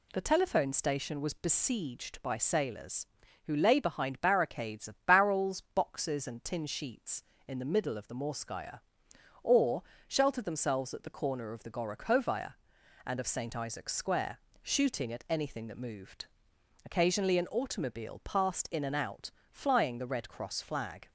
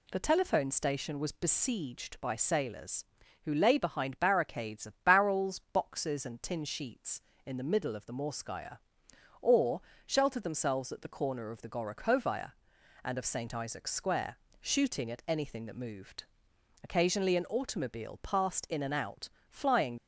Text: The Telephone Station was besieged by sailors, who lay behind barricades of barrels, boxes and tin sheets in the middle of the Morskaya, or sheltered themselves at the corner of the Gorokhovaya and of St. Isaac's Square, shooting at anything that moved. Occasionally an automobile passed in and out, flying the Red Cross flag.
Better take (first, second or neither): first